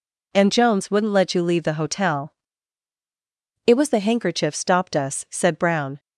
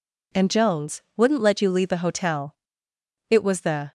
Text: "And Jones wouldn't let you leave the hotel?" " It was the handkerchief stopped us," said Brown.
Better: first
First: none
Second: pauses between "Jones" and "wouldn't"; slight; at 1.0 s; 0.16 s long // stops before "handkerchief stopped us said Brown"; at 3.8 s

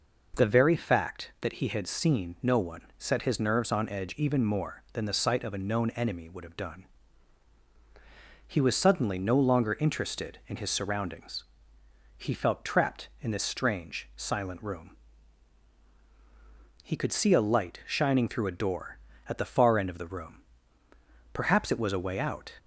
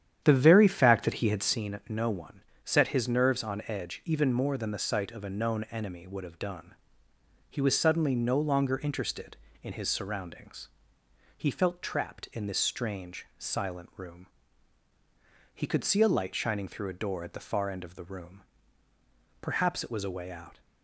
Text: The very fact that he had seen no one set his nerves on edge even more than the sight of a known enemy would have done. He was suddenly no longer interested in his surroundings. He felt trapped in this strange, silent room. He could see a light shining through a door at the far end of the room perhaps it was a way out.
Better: first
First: pauses between "one" and "set"; slight; at 2.8 s; 0.18 s long // pauses between "room" and "perhaps"; noticeable; at 20.4 s; 0.92 s long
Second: starts louder than the rest; strong; until 1.6 s; 9.5 dB // pauses between "one" and "set"; slight; at 2.4 s; 0.22 s long // pauses between "room" and "perhaps"; at 18.4 s; 1.0 s long

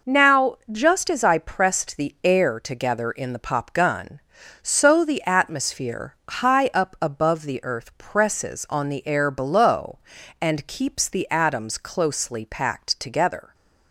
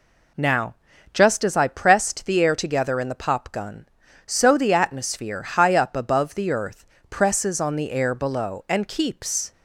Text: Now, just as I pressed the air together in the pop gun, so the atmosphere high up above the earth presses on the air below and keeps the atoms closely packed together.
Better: first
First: none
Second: pauses between "earth" and "presses"; slight; at 6.8 s; 0.24 s long // stops before "the atoms closely packed together"; at 9.5 s

